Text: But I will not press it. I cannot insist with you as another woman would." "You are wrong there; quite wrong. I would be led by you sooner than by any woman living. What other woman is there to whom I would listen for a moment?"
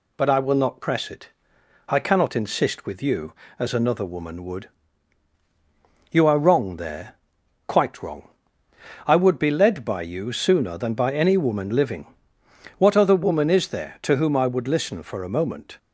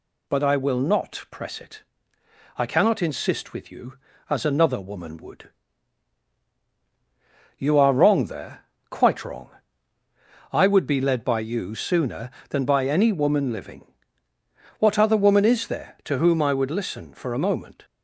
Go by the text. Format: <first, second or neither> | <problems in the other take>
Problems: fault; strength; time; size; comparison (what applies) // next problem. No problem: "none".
neither | none